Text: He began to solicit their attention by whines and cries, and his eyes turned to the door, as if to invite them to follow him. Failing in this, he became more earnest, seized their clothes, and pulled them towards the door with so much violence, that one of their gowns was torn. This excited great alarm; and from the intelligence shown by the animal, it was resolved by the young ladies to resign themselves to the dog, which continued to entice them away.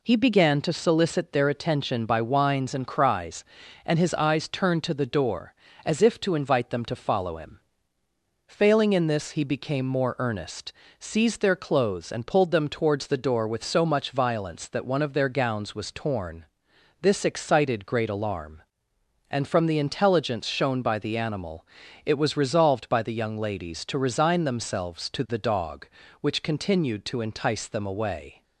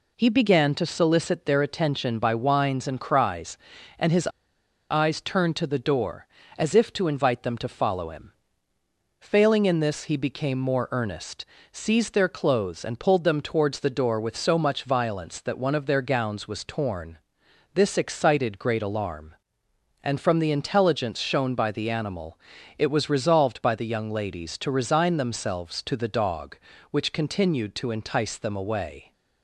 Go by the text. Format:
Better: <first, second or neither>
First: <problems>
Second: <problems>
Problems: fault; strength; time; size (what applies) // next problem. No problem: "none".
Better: first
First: none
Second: pauses between "his" and "eyes"; noticeable; at 4.2 s; 0.62 s long